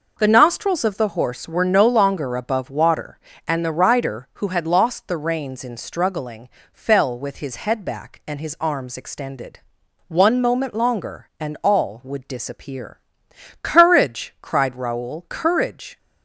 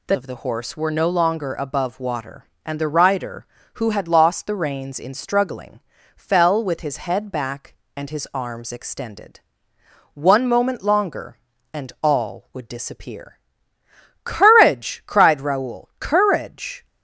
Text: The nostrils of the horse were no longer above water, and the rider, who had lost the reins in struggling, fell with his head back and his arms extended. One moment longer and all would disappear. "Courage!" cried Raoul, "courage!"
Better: first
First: none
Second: skips "nostrils"; at 0.1 s

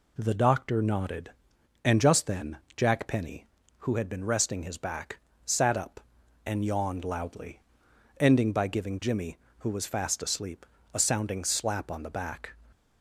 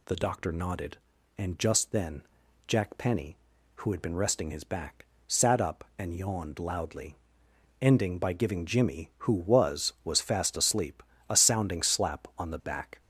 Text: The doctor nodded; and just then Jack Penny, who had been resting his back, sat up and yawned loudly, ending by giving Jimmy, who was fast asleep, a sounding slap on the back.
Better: first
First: pauses between "then" and "Jack"; slight; at 2.5 s; 0.18 s long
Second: pauses between "then" and "Jack"; at 2.2 s; 0.44 s long // says "was" twice; at 10.0 s

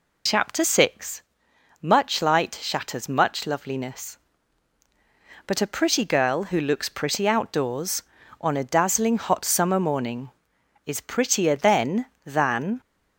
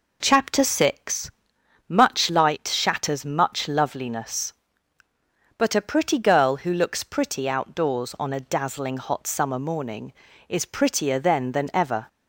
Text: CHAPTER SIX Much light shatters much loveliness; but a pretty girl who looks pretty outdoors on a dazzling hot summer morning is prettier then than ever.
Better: second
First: pauses between "SIX" and "Much"; noticeable; at 1.2 s; 0.62 s long // stops before "ever"; at 12.8 s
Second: pauses between "SIX" and "Much"; noticeable; at 1.3 s; 0.58 s long

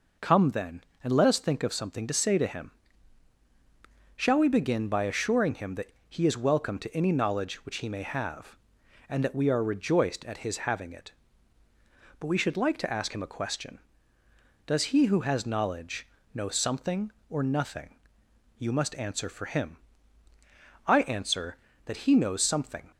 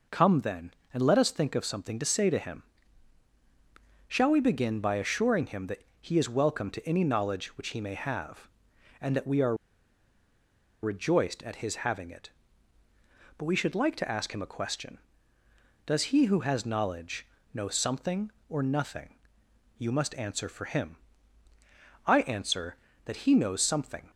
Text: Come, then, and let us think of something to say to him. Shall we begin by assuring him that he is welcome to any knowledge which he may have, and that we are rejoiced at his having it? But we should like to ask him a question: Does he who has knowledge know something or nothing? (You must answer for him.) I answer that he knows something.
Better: first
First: pauses between "that" and "he"; slight; at 5.9 s; 0.18 s long // pauses between "knowledge" and "know"; slight; at 16.0 s; 0.26 s long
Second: pauses between "that" and "he"; slight; at 5.8 s; 0.18 s long // pauses between "are" and "rejoiced"; strong; at 9.5 s; 1.2 s long // pauses between "knowledge" and "know"; slight; at 17.2 s; 0.26 s long

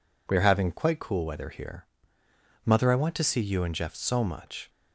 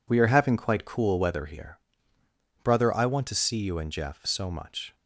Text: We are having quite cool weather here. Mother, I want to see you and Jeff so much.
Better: first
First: none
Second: says "Brother" for "Mother"; at 2.6 s

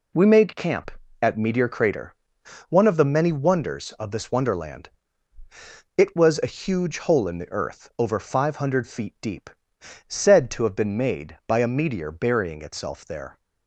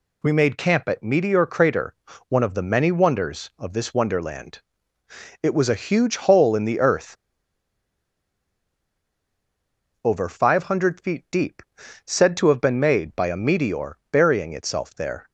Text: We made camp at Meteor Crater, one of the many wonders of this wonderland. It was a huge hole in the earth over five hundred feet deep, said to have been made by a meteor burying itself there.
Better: first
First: none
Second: pauses between "earth" and "over"; strong; at 7.1 s; 2.8 s long // pauses between "meteor" and "burying"; slight; at 13.9 s; 0.16 s long

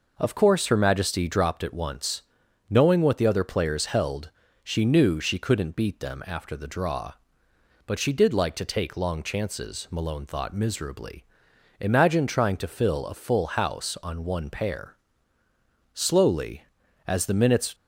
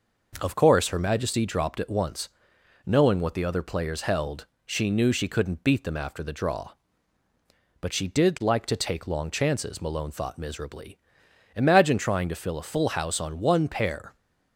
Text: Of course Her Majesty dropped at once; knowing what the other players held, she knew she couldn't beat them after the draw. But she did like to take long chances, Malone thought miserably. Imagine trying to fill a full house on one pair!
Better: second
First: goes on to say "Slowly as the minutes"; strong; from 15.9 s on; 1.8 s long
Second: none

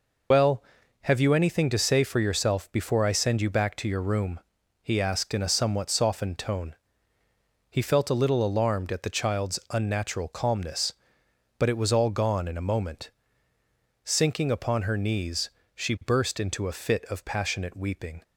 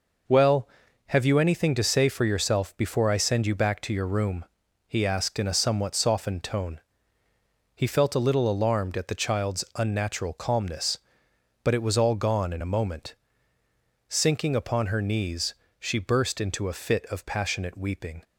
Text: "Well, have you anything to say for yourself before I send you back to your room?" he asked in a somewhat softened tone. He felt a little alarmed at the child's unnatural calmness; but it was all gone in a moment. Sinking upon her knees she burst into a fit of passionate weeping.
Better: second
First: loses the start of "Well"; at 0.3 s; 75 ms // pauses between "knees" and "she"; slight; at 15.5 s; 0.22 s long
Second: pauses between "knees" and "she"; slight; at 15.5 s; 0.22 s long

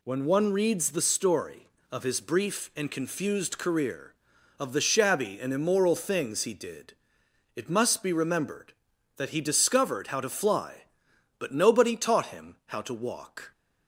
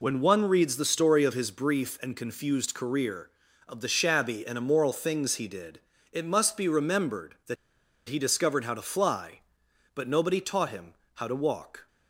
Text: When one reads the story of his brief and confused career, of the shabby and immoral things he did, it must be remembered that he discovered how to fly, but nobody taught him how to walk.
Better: first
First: none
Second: pauses between "that" and "he"; noticeable; at 7.5 s; 0.52 s long // pauses between "him" and "how"; slight; at 10.9 s; 0.22 s long

